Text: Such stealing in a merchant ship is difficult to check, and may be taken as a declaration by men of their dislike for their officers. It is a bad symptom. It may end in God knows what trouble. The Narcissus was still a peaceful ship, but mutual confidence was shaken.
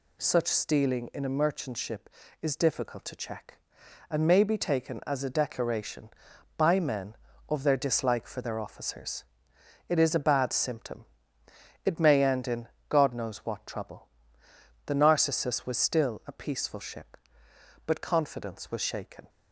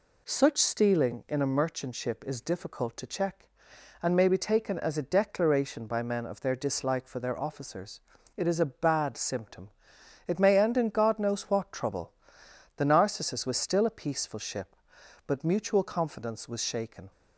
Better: second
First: pauses between "in" and "God"; slight; at 12.6 s; 0.22 s long // skips "mutual"; at 18.0 s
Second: none

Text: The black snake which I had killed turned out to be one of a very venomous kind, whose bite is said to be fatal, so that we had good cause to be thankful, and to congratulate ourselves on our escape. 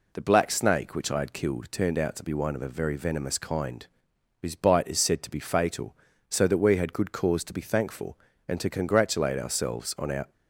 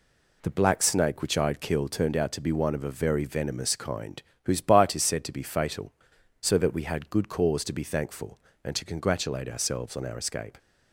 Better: second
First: stops before "escape"; at 10.3 s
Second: none

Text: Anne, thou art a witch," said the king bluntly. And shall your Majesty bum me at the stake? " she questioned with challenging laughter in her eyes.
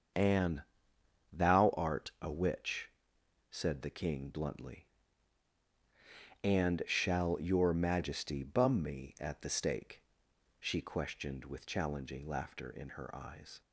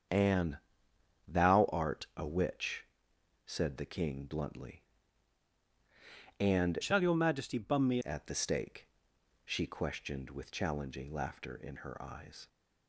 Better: first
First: starts louder than the rest; until 1.8 s; 7 dB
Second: starts louder than the rest; strong; until 1.7 s; 7.5 dB // changes voice from "shall" to "me"; from 6.8 to 7.9 s; 1.1 s long

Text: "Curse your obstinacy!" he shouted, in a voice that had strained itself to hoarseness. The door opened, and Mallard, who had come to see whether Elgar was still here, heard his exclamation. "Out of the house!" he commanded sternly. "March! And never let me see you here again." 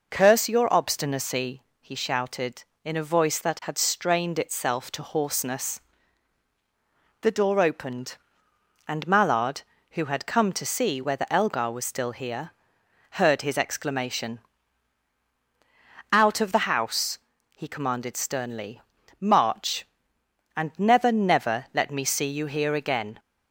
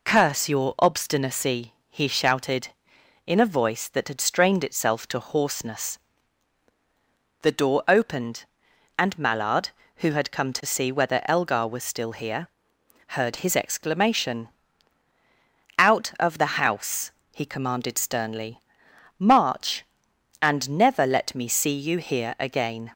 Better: second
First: says "never" twice; at 21.1 s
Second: none

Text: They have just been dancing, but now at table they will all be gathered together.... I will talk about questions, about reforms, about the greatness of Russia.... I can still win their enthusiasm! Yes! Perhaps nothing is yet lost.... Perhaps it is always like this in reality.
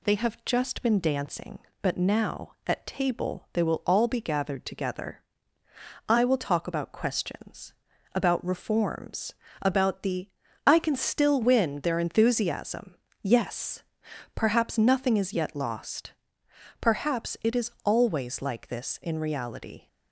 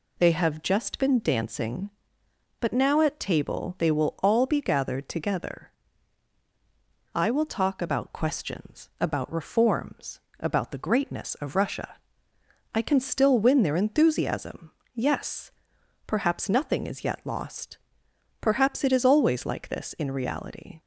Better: second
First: skips "greatness of Russia"; at 10.4 s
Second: none

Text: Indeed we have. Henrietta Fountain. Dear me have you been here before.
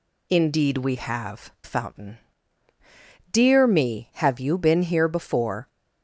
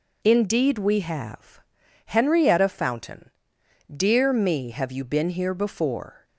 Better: second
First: skips "Henrietta"; at 1.5 s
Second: none

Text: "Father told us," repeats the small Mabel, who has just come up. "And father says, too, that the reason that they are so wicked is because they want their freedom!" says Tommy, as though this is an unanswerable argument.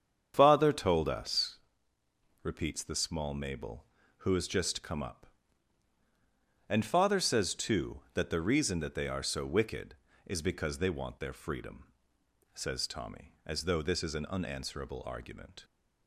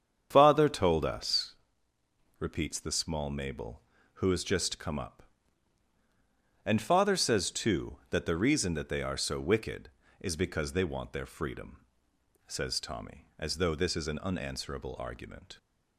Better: neither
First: starts louder than the rest; strong; until 1.4 s; 7.5 dB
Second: starts louder than the rest; strong; until 1.3 s; 7.5 dB

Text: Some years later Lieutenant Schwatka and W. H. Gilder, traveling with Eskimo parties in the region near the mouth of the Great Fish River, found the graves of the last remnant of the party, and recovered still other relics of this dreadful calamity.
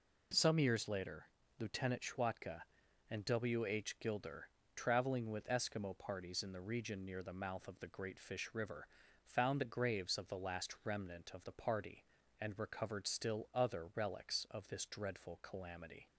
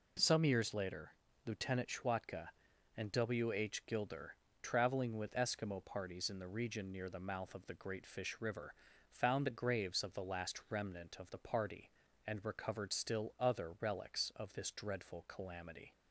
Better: neither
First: pauses between "later" and "Lieutenant"; slight; at 1.2 s; 0.30 s long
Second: pauses between "later" and "Lieutenant"; slight; at 1.1 s; 0.32 s long

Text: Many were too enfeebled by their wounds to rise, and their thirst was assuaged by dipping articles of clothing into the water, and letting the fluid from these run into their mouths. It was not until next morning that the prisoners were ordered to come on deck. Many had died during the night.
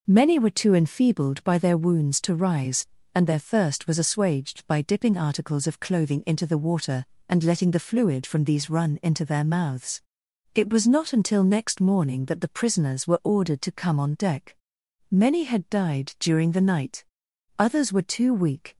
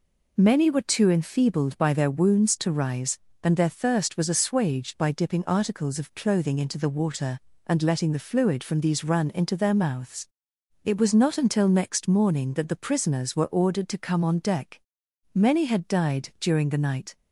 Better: second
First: goes on to say "Others were too weak"; noticeable; from 17.5 s on; 1.2 s long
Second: none

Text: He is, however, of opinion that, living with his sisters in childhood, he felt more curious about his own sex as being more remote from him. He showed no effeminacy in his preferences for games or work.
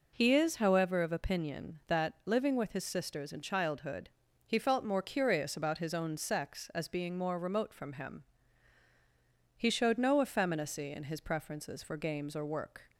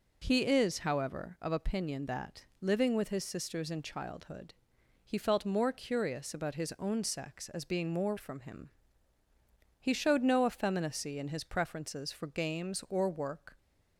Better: first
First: none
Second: skips "remote"; at 8.1 s

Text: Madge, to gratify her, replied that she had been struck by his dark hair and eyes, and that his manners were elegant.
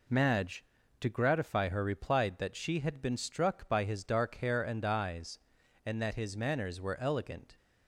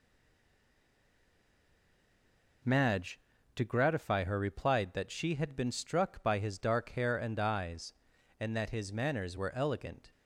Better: first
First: none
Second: stays silent before the first word; strong; until 2.6 s; 2.6 s long

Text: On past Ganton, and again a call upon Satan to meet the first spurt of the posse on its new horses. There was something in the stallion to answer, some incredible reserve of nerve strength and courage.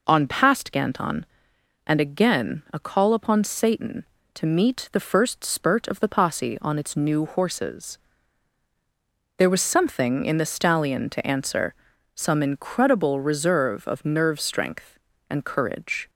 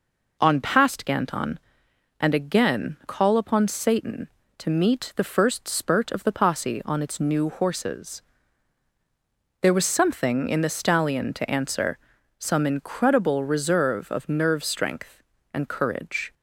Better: first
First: none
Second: skips "a"; at 3.0 s

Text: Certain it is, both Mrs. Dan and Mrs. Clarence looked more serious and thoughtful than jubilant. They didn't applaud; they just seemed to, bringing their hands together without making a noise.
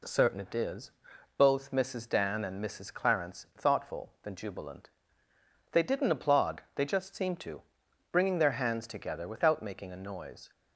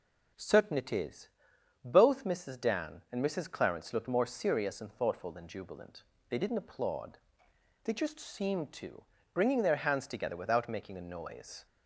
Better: second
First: skips "looked more serious and"; at 3.5 s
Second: none

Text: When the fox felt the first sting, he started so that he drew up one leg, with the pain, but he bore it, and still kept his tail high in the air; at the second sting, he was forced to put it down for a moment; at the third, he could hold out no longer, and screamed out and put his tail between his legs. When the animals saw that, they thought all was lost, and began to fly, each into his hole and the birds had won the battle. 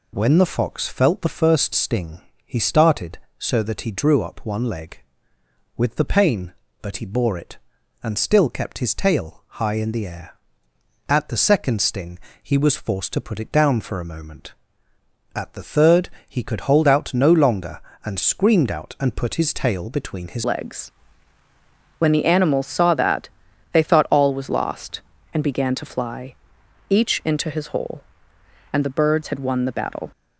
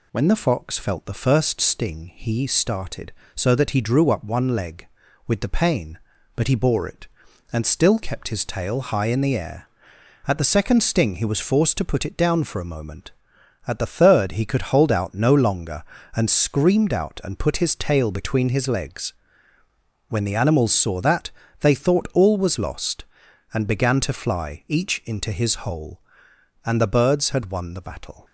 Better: second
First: pauses between "tail" and "high"; slight; at 9.4 s; 0.16 s long // changes voice at "legs"; from 20.4 s on; 9.7 s long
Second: none

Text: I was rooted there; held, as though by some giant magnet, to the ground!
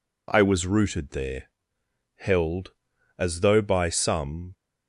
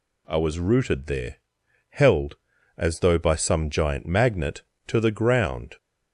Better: second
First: stops before "giant magnet to the ground"; at 4.5 s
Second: none

